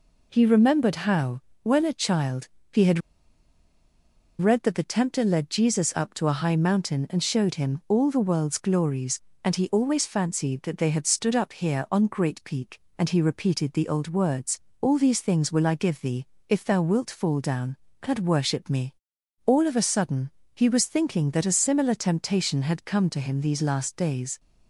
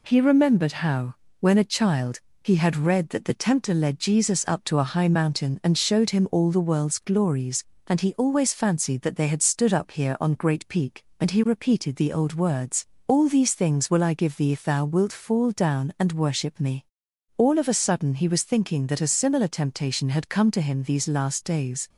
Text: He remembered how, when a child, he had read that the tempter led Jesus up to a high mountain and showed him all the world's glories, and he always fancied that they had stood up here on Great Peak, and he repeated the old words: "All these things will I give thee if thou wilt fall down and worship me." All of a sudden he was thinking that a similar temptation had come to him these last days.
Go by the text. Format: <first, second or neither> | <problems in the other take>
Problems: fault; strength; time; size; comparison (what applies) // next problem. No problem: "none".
second | pauses between "had" and "read"; strong; at 3.0 s; 1.4 s long // pauses between "thee" and "if"; slight; at 16.2 s; 0.22 s long // pauses between "sudden" and "he"; slight; at 20.2 s; 0.26 s long